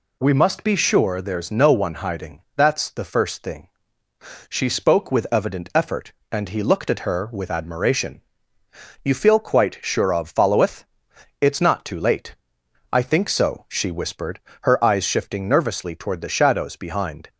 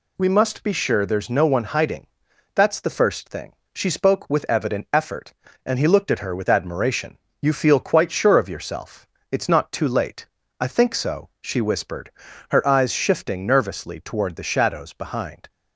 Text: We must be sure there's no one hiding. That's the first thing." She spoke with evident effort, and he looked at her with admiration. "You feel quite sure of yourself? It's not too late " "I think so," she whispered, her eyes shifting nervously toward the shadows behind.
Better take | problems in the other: second | says "followeth" for "yourself"; at 10.2 s

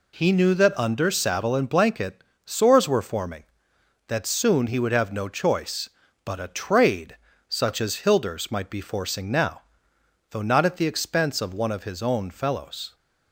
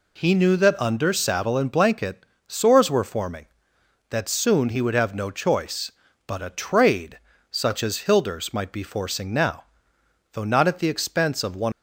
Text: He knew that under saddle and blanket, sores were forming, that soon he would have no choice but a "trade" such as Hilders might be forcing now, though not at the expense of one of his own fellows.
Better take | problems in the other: first | pauses between "trade" and "such"; slight; at 7.1 s; 0.32 s long; slight in the first // stops before "of his own fellows"; at 11.7 s

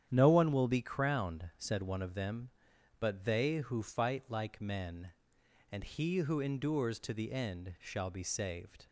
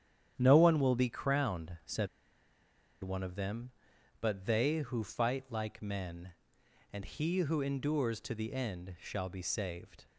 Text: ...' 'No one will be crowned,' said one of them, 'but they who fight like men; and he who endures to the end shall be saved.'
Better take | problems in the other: first | starts louder than the rest; strong; until 1.3 s; 9.5 dB; strong in the first // pauses between "said" and "one"; noticeable; at 2.0 s; 0.95 s long

